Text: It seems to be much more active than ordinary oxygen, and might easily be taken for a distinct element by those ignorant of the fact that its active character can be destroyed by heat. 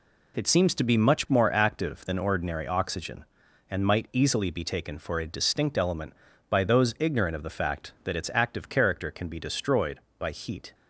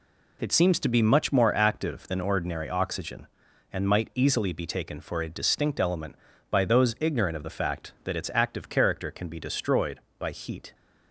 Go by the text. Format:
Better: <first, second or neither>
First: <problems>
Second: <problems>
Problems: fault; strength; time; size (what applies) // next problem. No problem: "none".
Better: neither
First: none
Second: none